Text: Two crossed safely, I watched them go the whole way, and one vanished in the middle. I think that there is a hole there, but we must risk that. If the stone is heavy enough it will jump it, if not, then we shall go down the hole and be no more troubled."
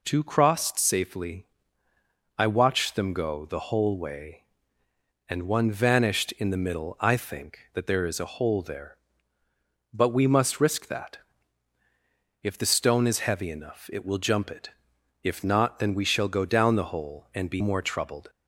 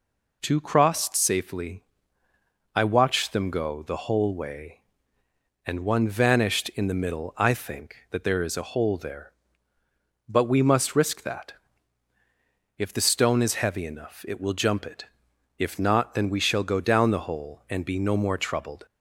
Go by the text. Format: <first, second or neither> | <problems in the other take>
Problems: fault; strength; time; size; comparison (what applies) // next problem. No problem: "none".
second | skips "no"; at 17.6 s